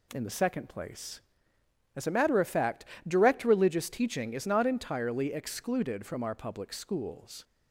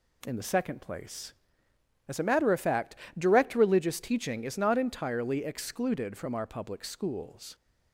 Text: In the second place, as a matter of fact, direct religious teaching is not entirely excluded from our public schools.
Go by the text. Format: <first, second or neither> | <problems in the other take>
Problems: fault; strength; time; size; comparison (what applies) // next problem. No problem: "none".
neither | none